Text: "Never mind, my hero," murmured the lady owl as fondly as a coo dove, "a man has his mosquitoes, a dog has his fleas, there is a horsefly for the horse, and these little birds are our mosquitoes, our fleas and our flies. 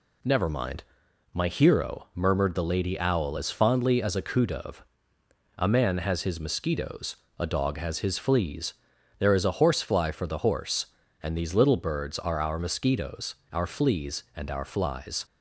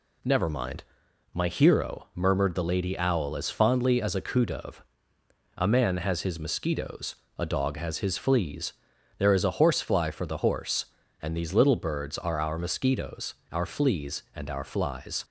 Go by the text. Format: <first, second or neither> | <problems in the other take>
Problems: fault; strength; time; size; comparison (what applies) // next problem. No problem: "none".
neither | none